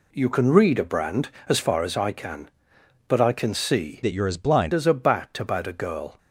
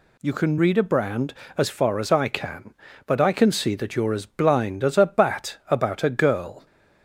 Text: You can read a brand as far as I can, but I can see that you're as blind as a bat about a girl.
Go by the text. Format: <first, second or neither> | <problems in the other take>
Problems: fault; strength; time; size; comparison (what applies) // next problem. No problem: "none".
second | changes voice from "that" to "blind"; from 4.0 to 4.7 s; 0.7 s long